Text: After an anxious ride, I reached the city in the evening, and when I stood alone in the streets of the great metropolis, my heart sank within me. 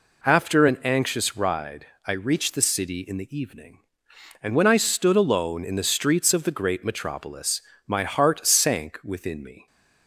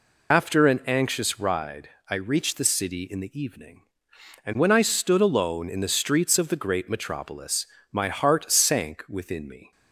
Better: first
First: none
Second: loses the start of "After"; at 0.3 s; 60 ms

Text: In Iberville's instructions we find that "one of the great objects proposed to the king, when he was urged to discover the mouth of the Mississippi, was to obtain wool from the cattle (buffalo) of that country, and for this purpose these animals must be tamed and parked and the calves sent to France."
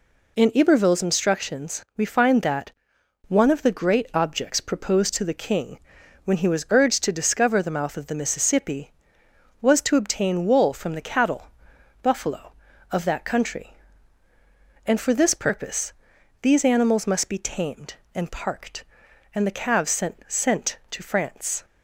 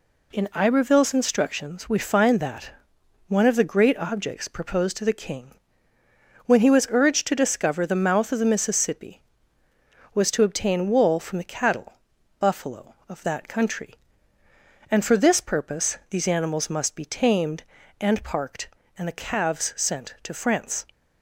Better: second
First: pauses between "that" and "one"; noticeable; at 2.7 s; 0.56 s long // pauses between "purpose" and "these"; noticeable; at 15.9 s; 0.50 s long // says "sent" twice; at 20.2 s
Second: pauses between "that" and "one"; noticeable; at 2.7 s; 0.58 s long

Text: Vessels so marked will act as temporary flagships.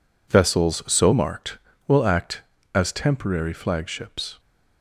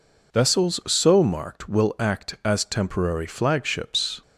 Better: neither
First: none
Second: none

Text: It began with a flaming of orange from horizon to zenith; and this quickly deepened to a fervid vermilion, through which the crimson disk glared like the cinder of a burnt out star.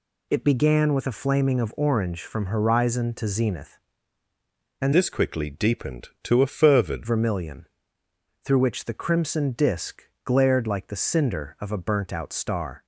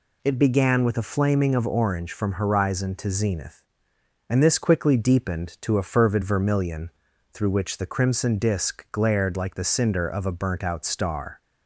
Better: second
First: changes voice from "this" to "fervid"; from 4.9 to 7.0 s; 2.1 s long // pauses between "disk" and "glared"; slight; at 10.0 s; 0.22 s long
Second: none

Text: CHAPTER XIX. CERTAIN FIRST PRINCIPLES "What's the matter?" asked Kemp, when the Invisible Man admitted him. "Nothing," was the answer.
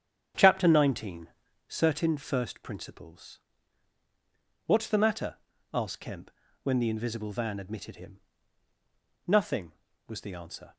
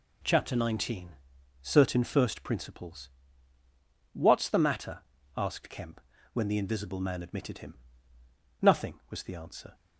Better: second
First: starts louder than the rest; strong; until 1.8 s; 9 dB // pauses between "PRINCIPLES" and "What's"; strong; at 3.3 s; 1.2 s long // says "Van" for "Man"; at 7.3 s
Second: pauses between "PRINCIPLES" and "What's"; at 3.0 s; 1.0 s long

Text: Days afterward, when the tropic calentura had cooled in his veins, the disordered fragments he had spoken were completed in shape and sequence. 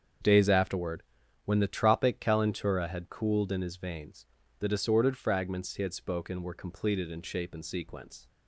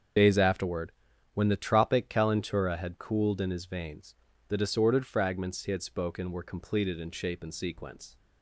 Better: first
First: starts louder than the rest; strong; until 1.6 s; 7.5 dB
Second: loses the start of "Days"; at 0.1 s; 65 ms // starts louder than the rest; until 1.6 s; 7 dB

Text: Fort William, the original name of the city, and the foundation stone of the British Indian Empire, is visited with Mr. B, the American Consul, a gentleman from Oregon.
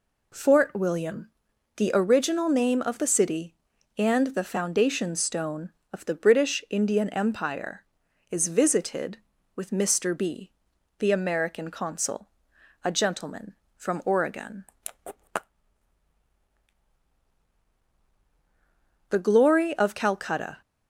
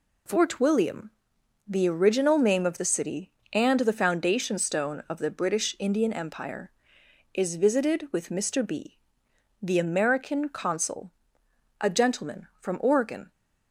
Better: second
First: goes on to say "The glory of Calcutta"; from 19.0 s on; 1.5 s long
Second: none

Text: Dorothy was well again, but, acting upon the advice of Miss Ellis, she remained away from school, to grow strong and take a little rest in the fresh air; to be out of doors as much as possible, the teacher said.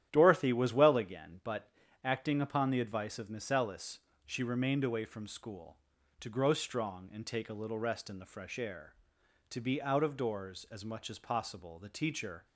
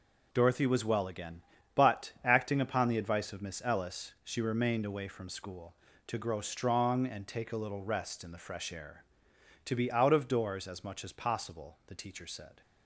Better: second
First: starts louder than the rest; strong; until 1.1 s; 11 dB // stops before "said"; at 12.4 s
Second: none

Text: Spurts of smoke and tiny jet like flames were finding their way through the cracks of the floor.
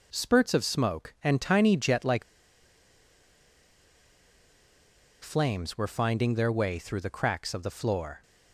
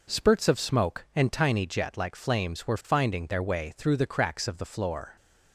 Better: second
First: pauses between "like" and "flames"; strong; at 2.2 s; 3.0 s long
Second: none

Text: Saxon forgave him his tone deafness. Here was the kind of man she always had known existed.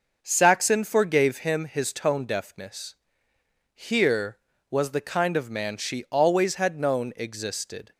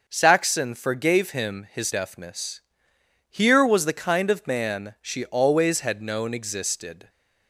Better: first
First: none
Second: starts louder than the rest; noticeable; until 1.0 s; 6 dB // skips "tone"; at 1.9 s

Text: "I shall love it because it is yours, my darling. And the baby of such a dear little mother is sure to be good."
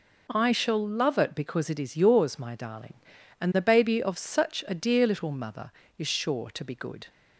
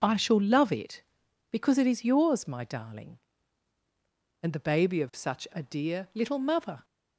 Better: first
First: none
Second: stops before "is sure to be good"; at 6.8 s

